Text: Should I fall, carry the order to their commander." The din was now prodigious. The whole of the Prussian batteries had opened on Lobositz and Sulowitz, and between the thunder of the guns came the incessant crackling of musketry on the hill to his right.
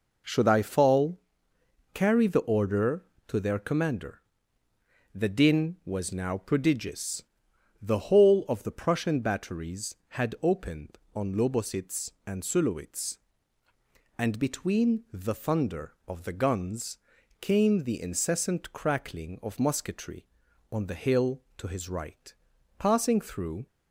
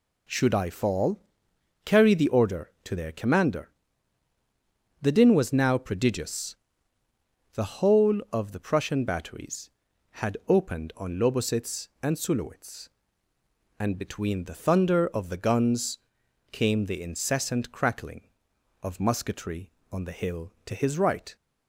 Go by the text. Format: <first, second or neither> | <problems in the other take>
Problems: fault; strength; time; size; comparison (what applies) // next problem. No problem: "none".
second | pauses between "guns" and "came"; at 16.9 s; 0.42 s long; noticeable in the second // goes on to say "Passing through"; noticeable; from 22.7 s on; 0.88 s long